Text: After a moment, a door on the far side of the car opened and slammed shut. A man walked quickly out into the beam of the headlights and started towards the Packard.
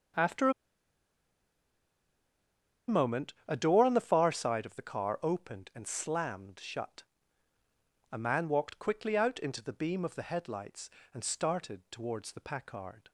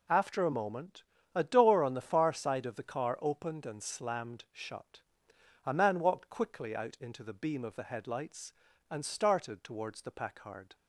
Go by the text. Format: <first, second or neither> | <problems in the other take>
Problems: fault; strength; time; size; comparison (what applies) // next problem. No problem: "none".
second | pauses between "a" and "moment"; strong; at 0.5 s; 2.3 s long